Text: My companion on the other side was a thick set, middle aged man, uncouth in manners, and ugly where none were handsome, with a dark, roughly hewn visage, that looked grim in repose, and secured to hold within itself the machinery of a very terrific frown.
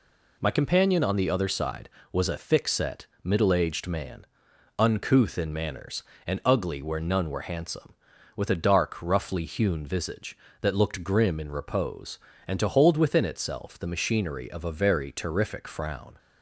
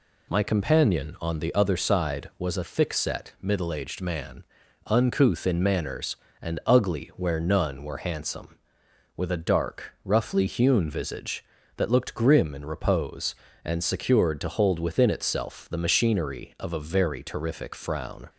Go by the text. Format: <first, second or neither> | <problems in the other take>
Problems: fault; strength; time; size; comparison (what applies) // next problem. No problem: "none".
second | skips "secured"; at 12.5 s